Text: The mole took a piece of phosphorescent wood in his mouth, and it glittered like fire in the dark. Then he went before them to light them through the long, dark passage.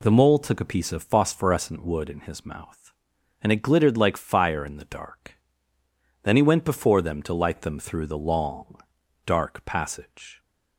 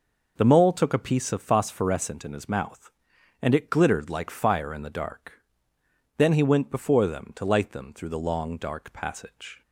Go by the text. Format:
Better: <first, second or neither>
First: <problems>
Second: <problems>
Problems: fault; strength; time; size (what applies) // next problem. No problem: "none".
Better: first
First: none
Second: skips "wood"; at 2.2 s